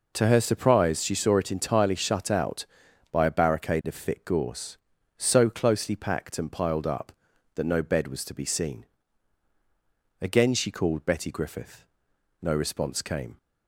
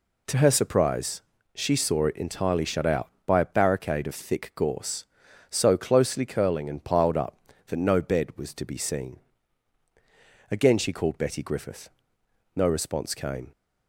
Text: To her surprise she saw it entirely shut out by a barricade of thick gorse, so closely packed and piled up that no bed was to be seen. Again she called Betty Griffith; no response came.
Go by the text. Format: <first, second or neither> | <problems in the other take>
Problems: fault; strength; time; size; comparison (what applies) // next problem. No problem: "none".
first | pauses between "surprise" and "she"; slight; at 1.2 s; 0.34 s long // says "curling" for "packed"; at 6.2 s